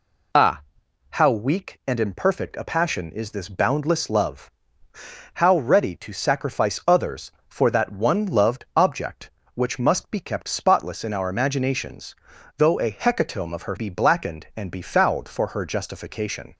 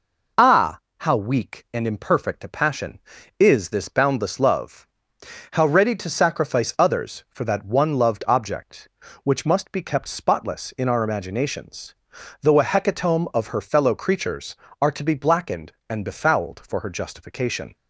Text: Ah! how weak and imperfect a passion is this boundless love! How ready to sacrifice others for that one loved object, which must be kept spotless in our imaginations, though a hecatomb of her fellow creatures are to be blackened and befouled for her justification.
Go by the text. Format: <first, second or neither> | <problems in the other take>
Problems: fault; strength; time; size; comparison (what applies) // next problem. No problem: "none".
second | skips "fellow creatures are to"; at 13.7 s